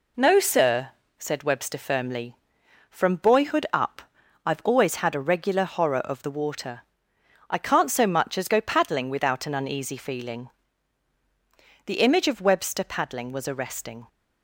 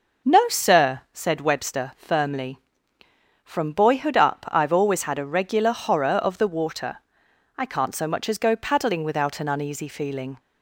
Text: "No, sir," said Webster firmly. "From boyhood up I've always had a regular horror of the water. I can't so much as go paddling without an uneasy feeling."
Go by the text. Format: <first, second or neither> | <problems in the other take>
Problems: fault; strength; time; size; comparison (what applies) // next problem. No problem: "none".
second | pauses between "up" and "I've"; at 4.0 s; 0.44 s long // goes on to say "The image of Webster paddling was arresting"; strong; from 11.8 s on; 2.2 s long